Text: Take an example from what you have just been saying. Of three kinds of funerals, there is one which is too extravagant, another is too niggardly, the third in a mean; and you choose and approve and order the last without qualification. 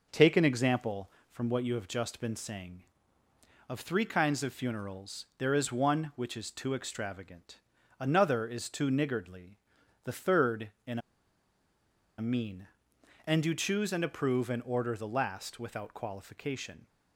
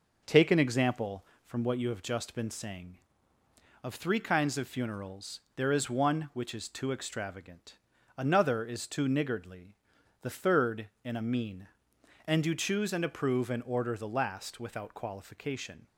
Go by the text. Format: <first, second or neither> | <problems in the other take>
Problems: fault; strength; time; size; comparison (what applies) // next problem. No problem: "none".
second | pauses between "in" and "a"; at 10.9 s; 1.1 s long